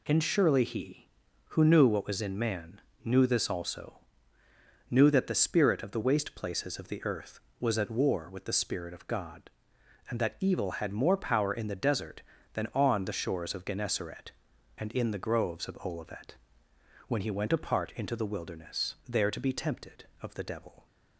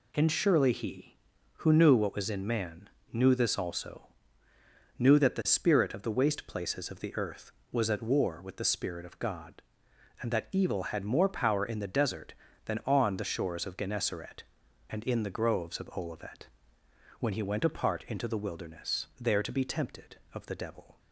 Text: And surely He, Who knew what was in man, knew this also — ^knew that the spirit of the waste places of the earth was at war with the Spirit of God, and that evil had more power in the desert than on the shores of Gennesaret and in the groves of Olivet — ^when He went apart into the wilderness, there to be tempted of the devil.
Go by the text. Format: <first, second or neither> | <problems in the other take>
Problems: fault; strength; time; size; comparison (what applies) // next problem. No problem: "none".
neither | none